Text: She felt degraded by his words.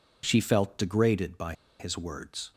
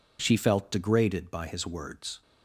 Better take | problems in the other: second | pauses between "by" and "his"; slight; at 1.5 s; 0.27 s long

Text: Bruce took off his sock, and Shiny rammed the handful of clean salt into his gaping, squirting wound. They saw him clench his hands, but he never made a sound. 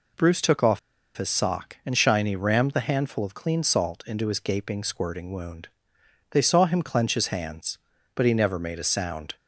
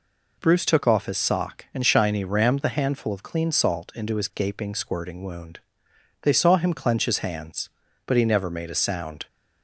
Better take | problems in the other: second | pauses between "off" and "his"; at 0.7 s; 0.38 s long

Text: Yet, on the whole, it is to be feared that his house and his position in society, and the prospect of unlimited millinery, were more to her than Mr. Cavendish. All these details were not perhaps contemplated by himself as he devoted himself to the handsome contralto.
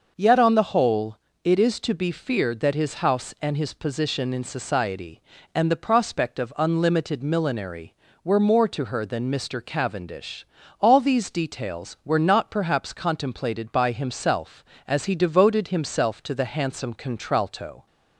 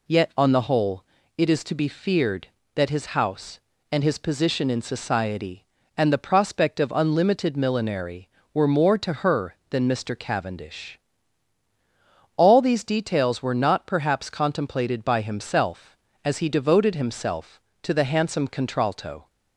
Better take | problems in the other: neither | none

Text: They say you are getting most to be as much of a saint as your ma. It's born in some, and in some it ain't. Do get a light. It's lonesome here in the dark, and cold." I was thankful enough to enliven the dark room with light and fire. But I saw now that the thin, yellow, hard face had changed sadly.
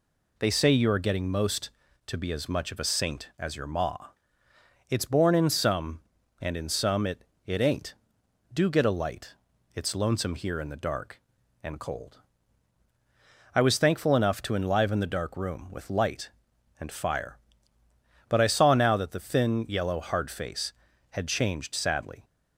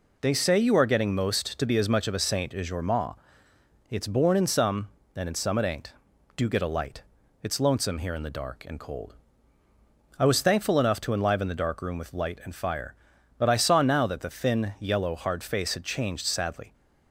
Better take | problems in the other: second | says "it" twice; at 7.4 s

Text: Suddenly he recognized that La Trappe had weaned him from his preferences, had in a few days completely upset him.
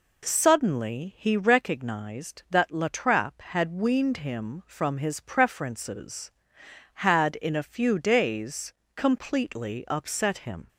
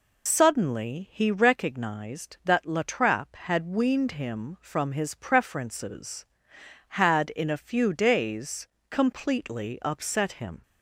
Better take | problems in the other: first | loses the start of "Suddenly"; at 0.2 s; 85 ms // pauses between "days" and "completely"; slight; at 8.6 s; 0.24 s long; slight in the first

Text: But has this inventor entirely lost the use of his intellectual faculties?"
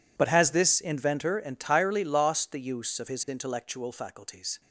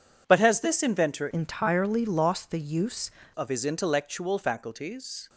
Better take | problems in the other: first | changes voice from "entirely" to "use"; from 1.2 to 3.0 s; 1.8 s long

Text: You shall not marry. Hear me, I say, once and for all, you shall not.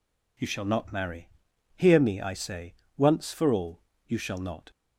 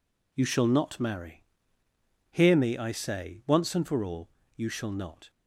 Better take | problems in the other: second | skips "and"; at 3.3 s

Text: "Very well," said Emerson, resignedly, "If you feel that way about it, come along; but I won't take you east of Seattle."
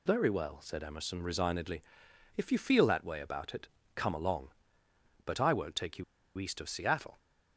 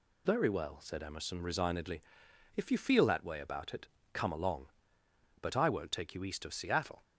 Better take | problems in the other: second | pauses between "you" and "east"; slight; at 6.0 s; 0.34 s long

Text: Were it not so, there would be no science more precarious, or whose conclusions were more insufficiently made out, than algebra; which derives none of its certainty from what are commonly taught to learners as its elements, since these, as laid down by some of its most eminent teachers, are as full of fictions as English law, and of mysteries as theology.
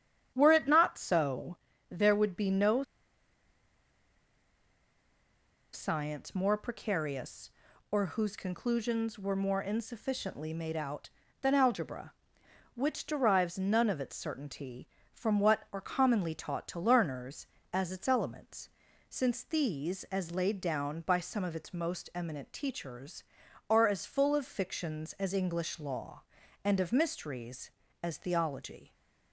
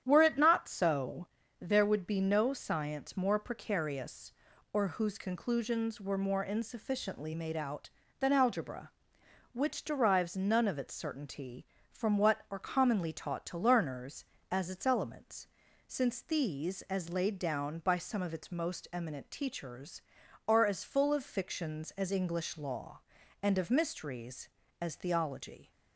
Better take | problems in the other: second | starts louder than the rest; strong; until 1.3 s; 9.5 dB; strong in the second // pauses between "no" and "science"; strong; at 2.8 s; 2.9 s long

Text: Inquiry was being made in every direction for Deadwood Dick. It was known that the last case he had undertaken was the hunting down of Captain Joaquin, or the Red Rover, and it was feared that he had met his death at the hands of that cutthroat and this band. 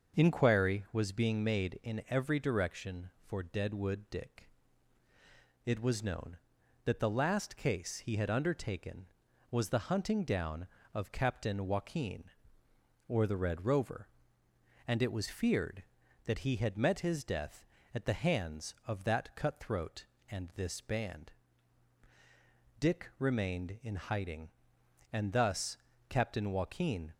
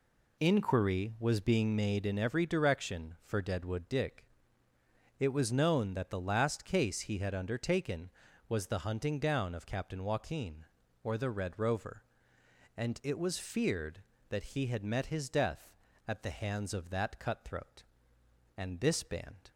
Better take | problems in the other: second | starts louder than the rest; until 1.2 s; 6.5 dB // goes on to say "Dick remained in hiding and thus Captain Joaquin"; strong; from 22.7 s on; 4.3 s long

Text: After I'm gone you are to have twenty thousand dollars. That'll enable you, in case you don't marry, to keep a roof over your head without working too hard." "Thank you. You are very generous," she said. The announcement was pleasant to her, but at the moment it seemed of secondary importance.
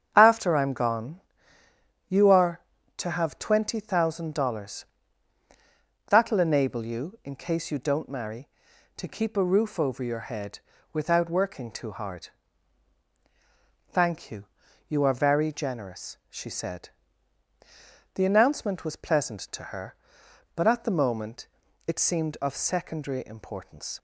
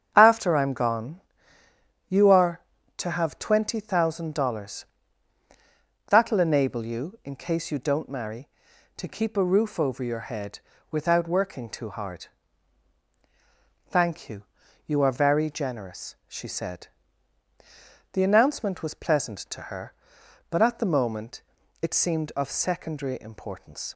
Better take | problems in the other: neither | starts louder than the rest; strong; the same in both // pauses between "gone" and "you"; noticeable; the same in both // pauses between "head" and "without"; slight; the same in both // pauses between "moment" and "it"; the same in both

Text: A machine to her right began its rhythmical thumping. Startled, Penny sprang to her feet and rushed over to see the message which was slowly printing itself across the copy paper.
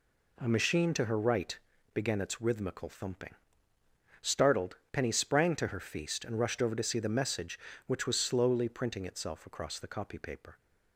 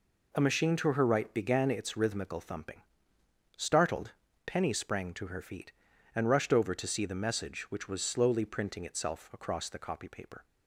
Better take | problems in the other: second | pauses between "right" and "began"; slight; at 1.5 s; 0.36 s long // says "feast" for "feet"; at 5.7 s

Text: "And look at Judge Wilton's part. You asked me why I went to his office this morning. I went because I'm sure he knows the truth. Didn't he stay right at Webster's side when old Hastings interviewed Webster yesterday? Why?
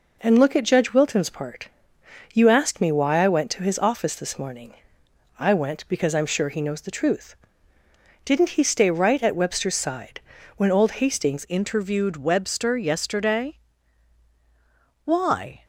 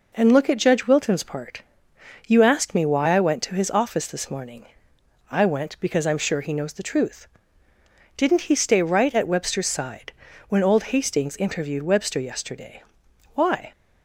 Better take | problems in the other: second | pauses between "side" and "when"; at 10.1 s; 0.38 s long; also in the second // changes voice at "interviewed"; from 11.4 s on; 4.2 s long

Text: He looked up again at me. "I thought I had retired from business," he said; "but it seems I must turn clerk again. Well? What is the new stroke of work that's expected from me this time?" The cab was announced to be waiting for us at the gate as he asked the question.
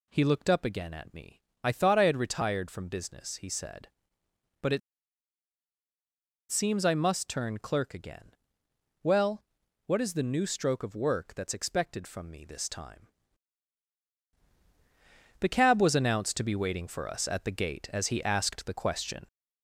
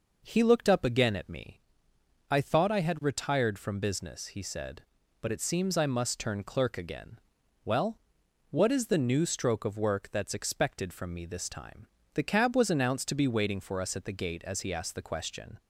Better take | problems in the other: second | pauses between "it" and "seems"; strong; at 4.8 s; 1.7 s long

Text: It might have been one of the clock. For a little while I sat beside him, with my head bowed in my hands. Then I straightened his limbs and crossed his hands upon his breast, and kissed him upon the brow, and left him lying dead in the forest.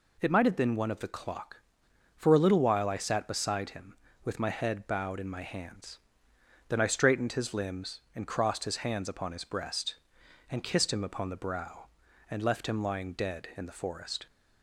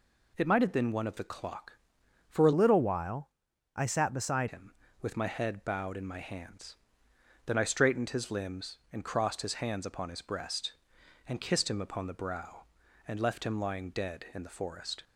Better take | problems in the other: first | changes voice from "little" to "beside"; from 2.5 to 4.4 s; 1.9 s long // pauses between "while" and "I"; noticeable; at 3.2 s; 0.46 s long

